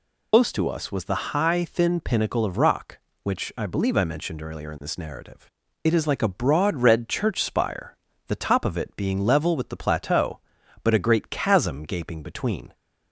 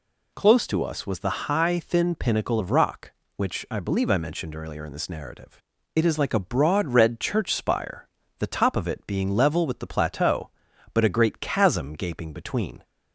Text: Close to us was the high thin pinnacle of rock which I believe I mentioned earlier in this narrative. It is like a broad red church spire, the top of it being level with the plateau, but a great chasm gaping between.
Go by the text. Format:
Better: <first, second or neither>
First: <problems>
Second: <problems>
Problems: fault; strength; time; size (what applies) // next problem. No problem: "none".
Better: second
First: loses the start of "Close"; at 0.3 s; 140 ms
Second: none